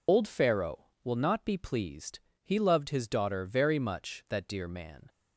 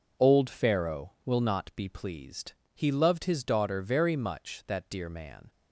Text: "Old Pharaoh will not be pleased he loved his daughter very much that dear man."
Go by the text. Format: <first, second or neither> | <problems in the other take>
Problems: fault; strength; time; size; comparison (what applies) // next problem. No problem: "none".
second | loses the start of "Old"; at 0.0 s; 100 ms // pauses between "pleased" and "he"; slight; at 2.1 s; 0.24 s long; slight in the second